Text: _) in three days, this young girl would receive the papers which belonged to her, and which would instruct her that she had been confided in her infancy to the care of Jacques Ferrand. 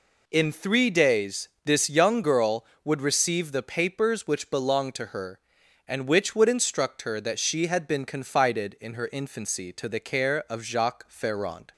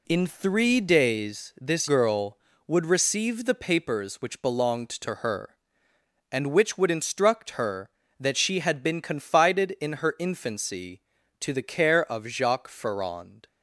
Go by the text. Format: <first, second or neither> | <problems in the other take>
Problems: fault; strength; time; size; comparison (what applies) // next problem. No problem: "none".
first | skips "young"; at 1.8 s